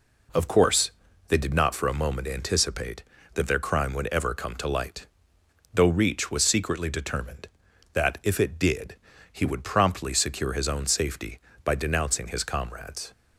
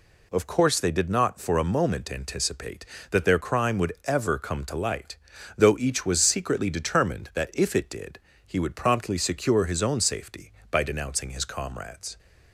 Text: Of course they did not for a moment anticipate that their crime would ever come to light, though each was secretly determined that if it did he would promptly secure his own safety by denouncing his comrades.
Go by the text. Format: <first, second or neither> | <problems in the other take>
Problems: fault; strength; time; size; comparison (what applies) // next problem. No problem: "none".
second | pauses between "course" and "they"; slight; at 0.9 s; 0.36 s long // says "reach" for "each"; at 5.8 s // pauses between "did" and "he"; slight; at 8.9 s; 0.36 s long; slight in the second